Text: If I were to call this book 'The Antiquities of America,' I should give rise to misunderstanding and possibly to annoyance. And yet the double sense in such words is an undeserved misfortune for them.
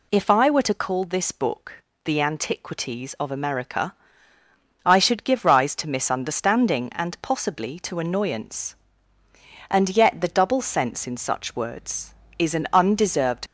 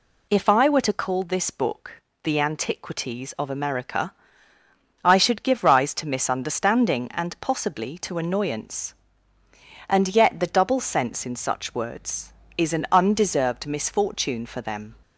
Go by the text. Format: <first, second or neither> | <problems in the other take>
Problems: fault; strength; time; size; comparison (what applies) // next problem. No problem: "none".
second | pauses between "book" and "The"; slight; at 1.8 s; 0.22 s long; slight in the second // stops before "misfortune for them"; at 13.4 s